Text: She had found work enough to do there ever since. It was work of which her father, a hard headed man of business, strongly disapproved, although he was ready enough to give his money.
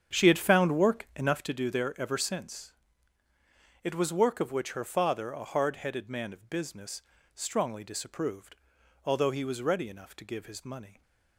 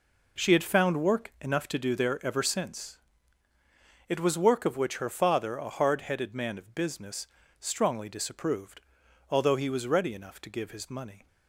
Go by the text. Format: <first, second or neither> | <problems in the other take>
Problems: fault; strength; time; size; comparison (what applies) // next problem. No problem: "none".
second | starts louder than the rest; strong; until 1.5 s; 8 dB